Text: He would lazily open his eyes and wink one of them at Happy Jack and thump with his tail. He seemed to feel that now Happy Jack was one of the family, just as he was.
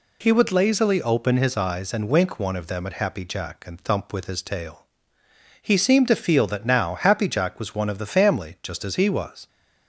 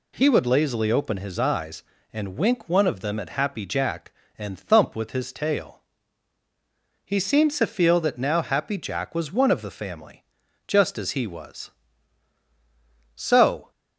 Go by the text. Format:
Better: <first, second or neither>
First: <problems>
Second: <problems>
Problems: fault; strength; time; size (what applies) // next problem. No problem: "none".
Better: first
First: none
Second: goes on to say "So"; from 13.1 s on; 0.54 s long